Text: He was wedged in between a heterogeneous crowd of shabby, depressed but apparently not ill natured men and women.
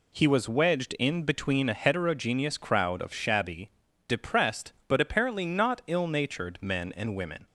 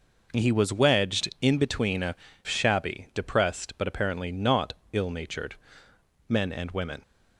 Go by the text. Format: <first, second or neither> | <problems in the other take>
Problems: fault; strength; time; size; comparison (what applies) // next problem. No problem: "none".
first | skips "heterogeneous crowd of"; at 2.3 s // pauses between "not" and "ill"; slight; at 4.7 s; 0.18 s long // pauses between "natured" and "men"; noticeable; at 5.5 s; 0.74 s long